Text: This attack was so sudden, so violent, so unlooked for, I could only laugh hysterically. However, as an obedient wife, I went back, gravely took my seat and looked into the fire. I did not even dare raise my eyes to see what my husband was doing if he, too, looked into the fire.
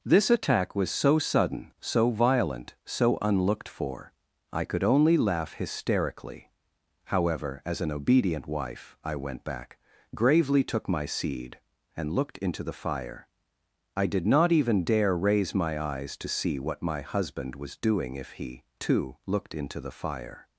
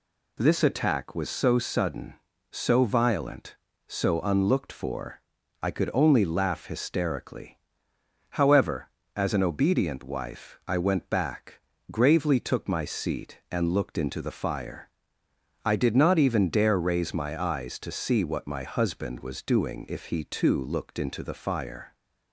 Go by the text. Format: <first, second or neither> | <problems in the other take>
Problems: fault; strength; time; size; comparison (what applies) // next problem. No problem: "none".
second | says "seed" for "seat"; at 11.0 s